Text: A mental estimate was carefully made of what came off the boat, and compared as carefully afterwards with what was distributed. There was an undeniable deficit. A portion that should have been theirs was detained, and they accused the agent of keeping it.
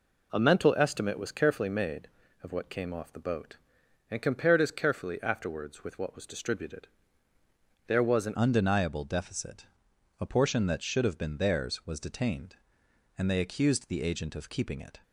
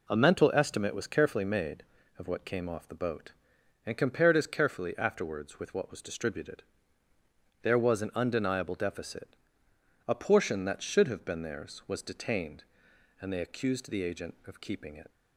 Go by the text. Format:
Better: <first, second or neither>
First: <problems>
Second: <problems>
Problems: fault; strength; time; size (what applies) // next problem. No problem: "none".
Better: second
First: changes voice at "undeniable"; from 8.3 s on; 6.6 s long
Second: none